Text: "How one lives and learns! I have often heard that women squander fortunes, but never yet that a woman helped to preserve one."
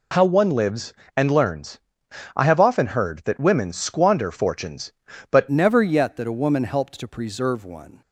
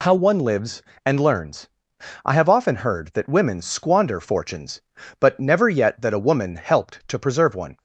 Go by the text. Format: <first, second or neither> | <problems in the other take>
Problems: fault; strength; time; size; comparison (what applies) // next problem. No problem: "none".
second | changes voice at "never"; from 5.5 s on; 2.5 s long